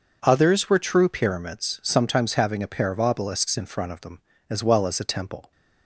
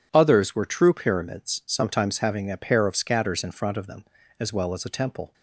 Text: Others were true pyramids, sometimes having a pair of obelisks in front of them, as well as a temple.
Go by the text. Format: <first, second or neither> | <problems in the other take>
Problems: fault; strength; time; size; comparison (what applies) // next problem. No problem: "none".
first | says "scatters" for "obelisks"; at 2.9 s